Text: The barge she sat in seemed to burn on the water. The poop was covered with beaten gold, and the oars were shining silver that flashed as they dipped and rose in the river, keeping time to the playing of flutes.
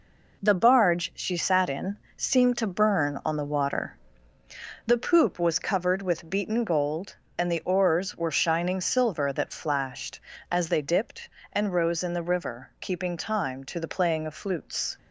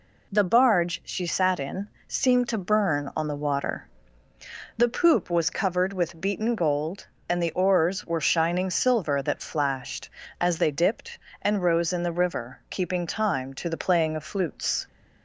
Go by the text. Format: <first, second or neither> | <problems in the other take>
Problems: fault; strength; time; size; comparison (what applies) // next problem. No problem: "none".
second | gets quieter; throughout; 6.5 dB // pauses between "in" and "seemed"; slight; at 1.9 s; 0.18 s long; slight in the second